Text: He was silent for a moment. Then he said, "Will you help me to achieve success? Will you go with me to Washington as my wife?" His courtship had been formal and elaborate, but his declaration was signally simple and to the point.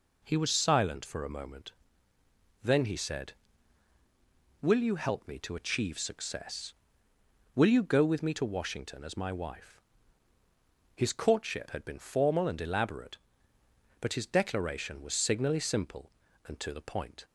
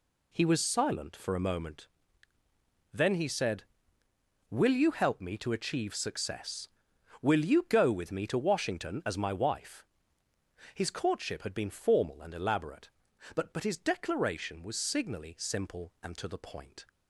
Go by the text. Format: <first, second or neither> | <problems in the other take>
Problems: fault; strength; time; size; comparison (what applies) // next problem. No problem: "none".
first | says "but" twice; at 13.5 s